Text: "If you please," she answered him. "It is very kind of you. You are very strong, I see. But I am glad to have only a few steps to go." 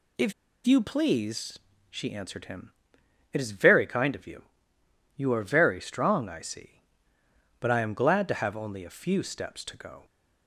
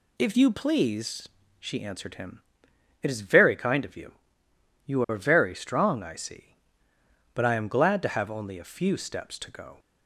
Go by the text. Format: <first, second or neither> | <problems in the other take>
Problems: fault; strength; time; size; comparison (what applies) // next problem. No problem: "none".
second | pauses between "If" and "you"; slight; at 0.3 s; 0.31 s long